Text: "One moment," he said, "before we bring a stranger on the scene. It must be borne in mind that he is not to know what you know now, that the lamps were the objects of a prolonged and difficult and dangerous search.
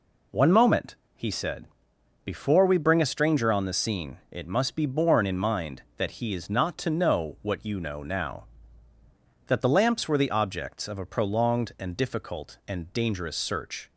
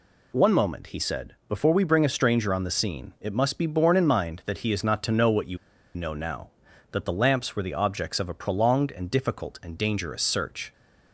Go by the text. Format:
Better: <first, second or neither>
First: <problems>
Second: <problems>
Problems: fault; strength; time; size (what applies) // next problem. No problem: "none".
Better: first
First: none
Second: pauses between "you" and "know"; at 5.5 s; 0.38 s long